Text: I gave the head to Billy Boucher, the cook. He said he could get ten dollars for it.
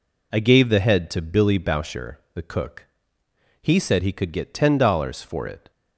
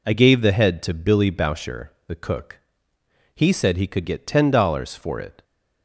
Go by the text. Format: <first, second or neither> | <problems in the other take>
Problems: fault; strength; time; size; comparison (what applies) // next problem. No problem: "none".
neither | none